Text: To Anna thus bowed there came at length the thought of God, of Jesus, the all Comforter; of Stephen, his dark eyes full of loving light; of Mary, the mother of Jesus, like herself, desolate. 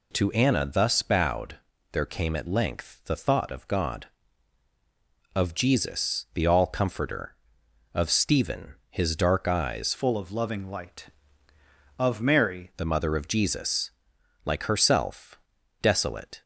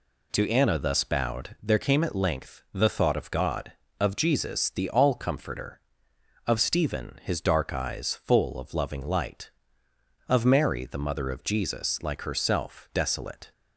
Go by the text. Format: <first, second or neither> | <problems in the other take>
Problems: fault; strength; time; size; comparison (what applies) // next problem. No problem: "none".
second | pauses between "bowed" and "there"; slight; at 1.5 s; 0.34 s long // changes voice from "full" to "Mary"; from 9.9 to 12.7 s; 2.8 s long